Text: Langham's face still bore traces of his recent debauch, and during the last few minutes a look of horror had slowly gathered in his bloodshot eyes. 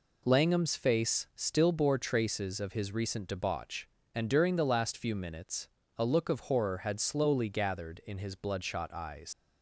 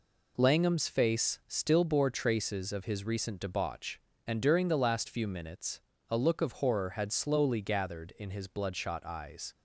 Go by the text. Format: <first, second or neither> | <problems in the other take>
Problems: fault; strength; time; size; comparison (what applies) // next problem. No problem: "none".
second | pauses between "minutes" and "a"; slight; at 5.6 s; 0.30 s long; slight in the second // leaves "eyes" unfinished; at 9.3 s; 90 ms